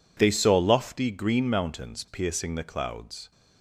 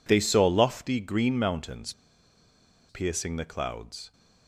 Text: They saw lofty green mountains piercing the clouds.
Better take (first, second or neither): first